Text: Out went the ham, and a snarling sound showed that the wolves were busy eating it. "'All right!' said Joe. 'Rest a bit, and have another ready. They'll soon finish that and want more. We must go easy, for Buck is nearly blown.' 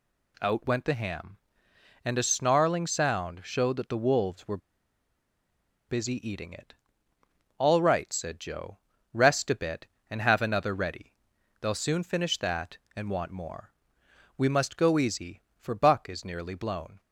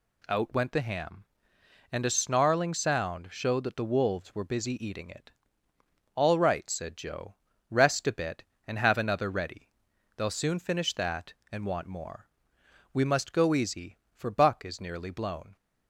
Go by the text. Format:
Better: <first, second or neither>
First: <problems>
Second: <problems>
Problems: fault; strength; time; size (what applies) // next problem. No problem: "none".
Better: second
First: pauses between "were" and "busy"; strong; at 4.5 s; 1.3 s long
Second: none